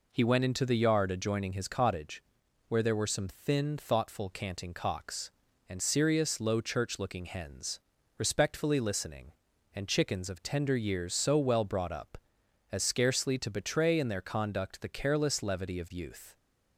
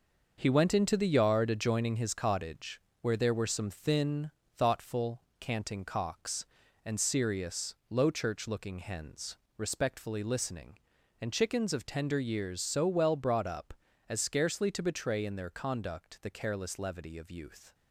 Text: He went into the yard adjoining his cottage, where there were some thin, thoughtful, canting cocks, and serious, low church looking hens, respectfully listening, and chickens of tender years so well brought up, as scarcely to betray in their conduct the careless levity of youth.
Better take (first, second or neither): first